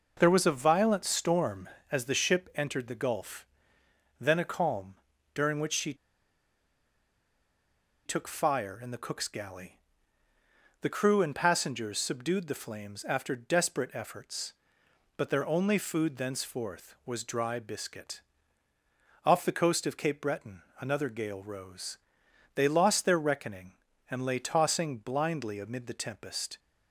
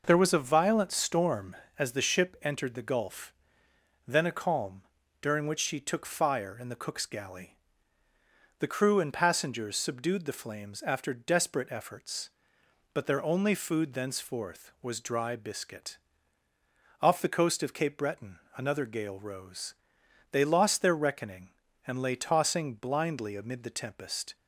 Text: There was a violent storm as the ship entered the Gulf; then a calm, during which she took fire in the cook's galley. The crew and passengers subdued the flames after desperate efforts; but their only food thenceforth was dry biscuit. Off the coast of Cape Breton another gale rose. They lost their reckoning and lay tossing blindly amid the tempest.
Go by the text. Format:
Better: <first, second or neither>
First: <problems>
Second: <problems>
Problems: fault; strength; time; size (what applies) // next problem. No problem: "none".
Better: second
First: pauses between "she" and "took"; strong; at 5.9 s; 2.1 s long // pauses between "Breton" and "another"; slight; at 20.6 s; 0.18 s long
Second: pauses between "Breton" and "another"; slight; at 18.3 s; 0.18 s long